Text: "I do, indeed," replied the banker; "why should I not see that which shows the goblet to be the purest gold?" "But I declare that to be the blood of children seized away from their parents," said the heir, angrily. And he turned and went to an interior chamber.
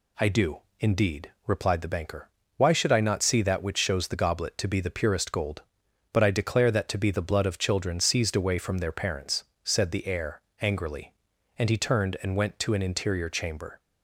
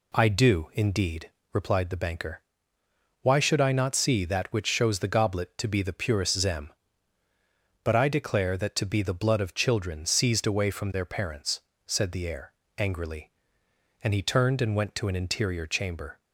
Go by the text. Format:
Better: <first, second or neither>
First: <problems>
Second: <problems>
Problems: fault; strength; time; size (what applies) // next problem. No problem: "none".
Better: first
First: none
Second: says "zem" for "gold"; at 6.3 s